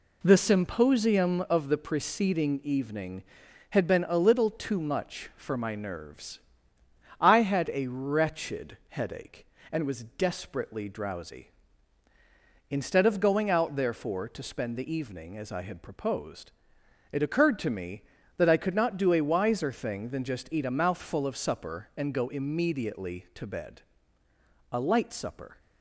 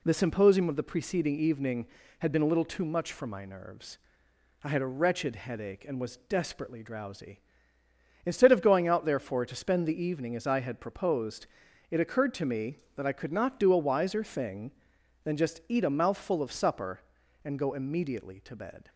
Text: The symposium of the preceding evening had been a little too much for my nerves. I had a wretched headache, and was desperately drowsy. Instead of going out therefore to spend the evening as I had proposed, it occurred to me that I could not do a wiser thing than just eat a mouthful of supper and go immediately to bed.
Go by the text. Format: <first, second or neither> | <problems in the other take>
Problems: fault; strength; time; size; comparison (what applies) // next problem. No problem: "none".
second | goes on to say "A light supper"; noticeable; from 24.7 s on; 0.86 s long